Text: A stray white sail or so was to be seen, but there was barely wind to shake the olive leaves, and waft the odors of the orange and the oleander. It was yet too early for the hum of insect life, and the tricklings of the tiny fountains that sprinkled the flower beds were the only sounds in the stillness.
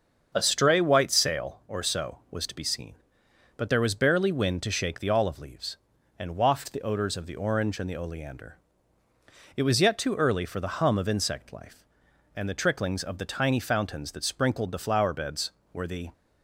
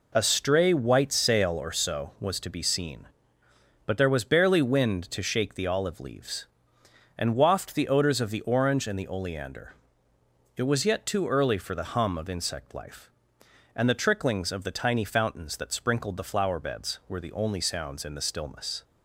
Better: second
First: starts louder than the rest; until 1.3 s; 7 dB // stops before "only sounds in the stillness"; at 16.1 s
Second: none

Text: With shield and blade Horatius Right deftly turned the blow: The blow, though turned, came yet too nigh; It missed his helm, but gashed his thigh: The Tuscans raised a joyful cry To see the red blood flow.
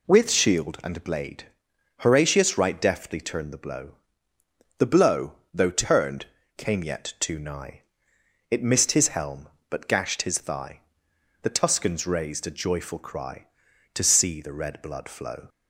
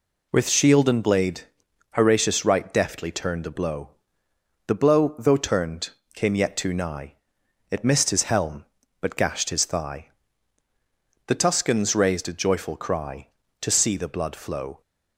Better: first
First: pauses between "blade" and "Horatius"; noticeable; at 1.4 s; 0.56 s long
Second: pauses between "blade" and "Horatius"; noticeable; at 1.4 s; 0.50 s long // skips "red"; at 14.0 s

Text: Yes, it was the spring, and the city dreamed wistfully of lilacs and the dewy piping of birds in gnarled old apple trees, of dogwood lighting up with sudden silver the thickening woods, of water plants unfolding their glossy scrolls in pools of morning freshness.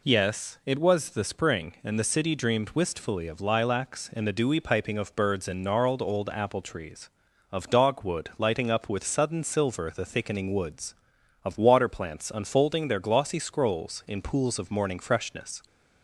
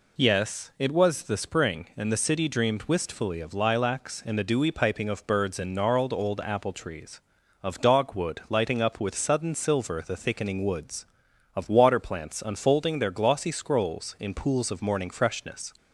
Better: neither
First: none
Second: none

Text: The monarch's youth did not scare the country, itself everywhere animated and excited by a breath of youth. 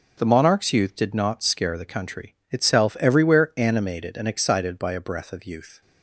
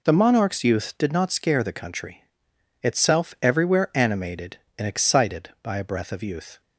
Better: neither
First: none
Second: none

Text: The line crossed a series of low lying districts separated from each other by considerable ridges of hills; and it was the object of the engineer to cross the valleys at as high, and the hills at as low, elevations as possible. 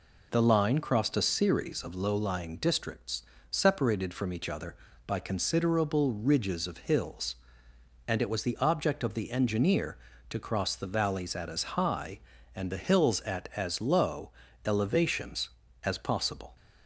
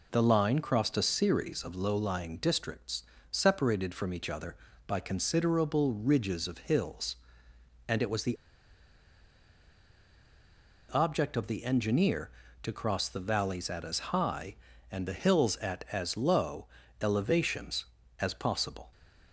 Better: first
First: pauses between "districts" and "separated"; slight; at 3.2 s; 0.26 s long // pauses between "as" and "high"; slight; at 11.6 s; 0.16 s long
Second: pauses between "districts" and "separated"; slight; at 3.0 s; 0.26 s long // pauses between "the" and "object"; strong; at 8.3 s; 2.5 s long // pauses between "as" and "high"; slight; at 13.9 s; 0.16 s long

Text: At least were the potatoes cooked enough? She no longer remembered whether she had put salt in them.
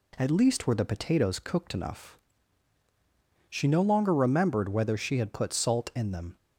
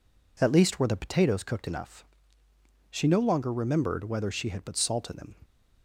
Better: neither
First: none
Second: none

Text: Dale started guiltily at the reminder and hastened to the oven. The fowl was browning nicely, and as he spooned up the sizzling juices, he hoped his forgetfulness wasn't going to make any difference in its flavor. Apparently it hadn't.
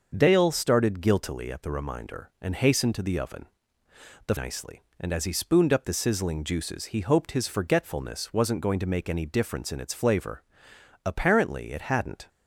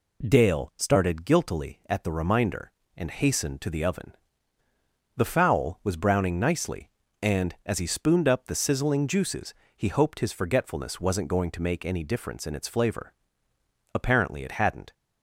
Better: second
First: starts louder than the rest; until 1.1 s; 6.5 dB // skips "fowl was browning"; at 4.3 s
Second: none

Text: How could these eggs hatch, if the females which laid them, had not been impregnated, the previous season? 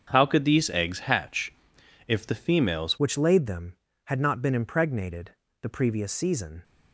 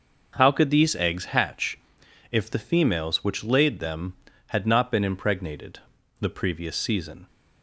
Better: second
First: starts louder than the rest; until 1.1 s; 7 dB // changes voice at "which"; from 2.9 s on; 3.7 s long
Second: none

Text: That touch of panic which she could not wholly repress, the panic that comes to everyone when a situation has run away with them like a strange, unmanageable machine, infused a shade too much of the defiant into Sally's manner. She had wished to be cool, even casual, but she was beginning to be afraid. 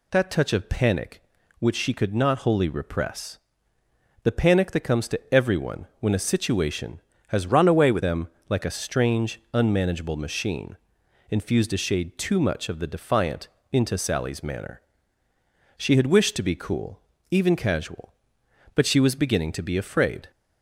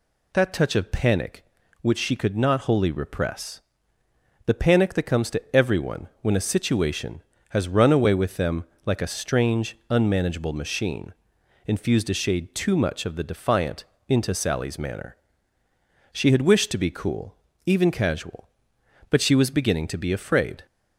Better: second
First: changes voice from "run" to "with"; from 7.5 to 8.0 s; 0.5 s long // pauses between "them" and "like"; slight; at 8.2 s; 0.20 s long // pauses between "defiant" and "into"; slight; at 13.4 s; 0.24 s long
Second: pauses between "them" and "like"; slight; at 8.6 s; 0.20 s long // pauses between "defiant" and "into"; slight; at 13.8 s; 0.24 s long

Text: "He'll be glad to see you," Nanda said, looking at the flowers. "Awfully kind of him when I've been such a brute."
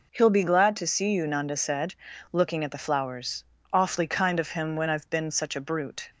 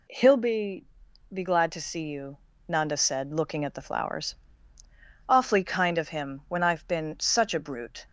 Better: first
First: none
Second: says "be" twice; at 1.3 s

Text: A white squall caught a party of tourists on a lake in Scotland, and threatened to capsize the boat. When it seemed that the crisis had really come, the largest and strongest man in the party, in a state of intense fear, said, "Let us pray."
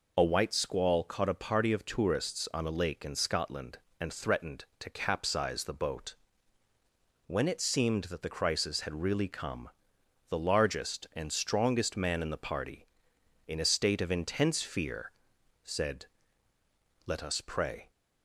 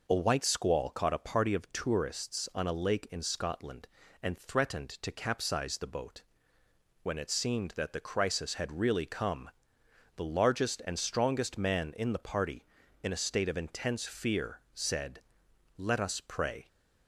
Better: neither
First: none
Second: none

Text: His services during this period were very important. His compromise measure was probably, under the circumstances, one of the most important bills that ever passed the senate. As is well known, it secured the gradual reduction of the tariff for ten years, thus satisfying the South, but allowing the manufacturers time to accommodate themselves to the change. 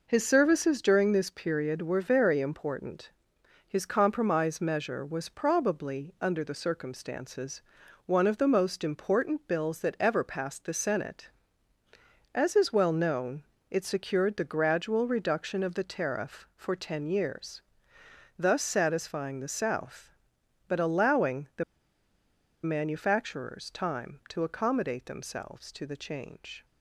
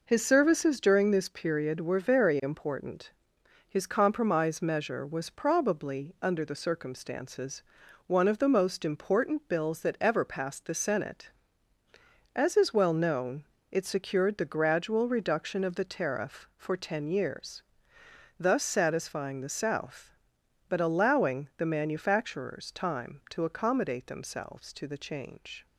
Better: second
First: pauses between "the" and "manufacturers"; at 21.6 s; 1.0 s long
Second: none

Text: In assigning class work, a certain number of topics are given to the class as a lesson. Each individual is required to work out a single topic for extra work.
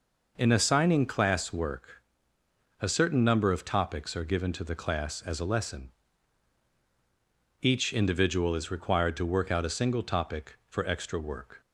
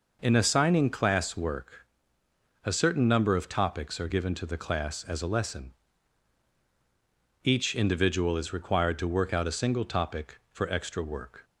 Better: neither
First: none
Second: none

